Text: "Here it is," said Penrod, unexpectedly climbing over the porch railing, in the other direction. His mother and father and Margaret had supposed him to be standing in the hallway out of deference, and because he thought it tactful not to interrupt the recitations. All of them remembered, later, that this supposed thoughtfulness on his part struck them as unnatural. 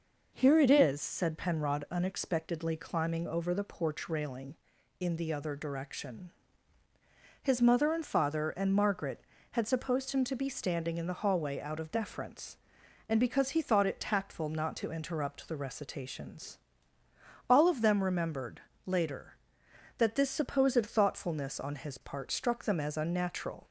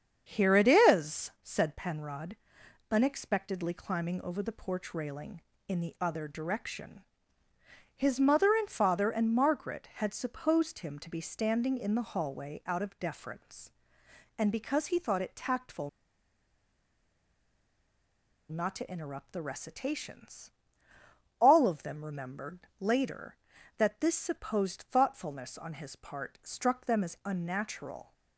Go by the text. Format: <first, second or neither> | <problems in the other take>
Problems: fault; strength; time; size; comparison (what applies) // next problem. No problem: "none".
first | starts louder than the rest; strong; until 1.3 s; 7.5 dB // pauses between "tactful" and "not"; strong; at 15.8 s; 2.6 s long